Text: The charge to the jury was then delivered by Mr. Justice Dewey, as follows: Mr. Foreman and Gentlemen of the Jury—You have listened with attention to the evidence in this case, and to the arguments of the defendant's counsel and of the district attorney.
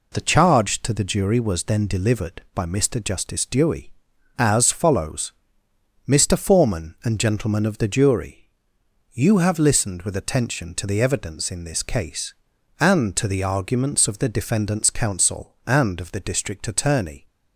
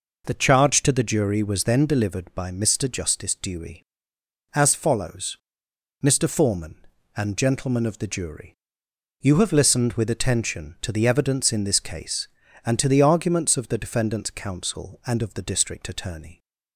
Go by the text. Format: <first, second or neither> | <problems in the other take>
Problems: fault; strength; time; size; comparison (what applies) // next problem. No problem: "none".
neither | none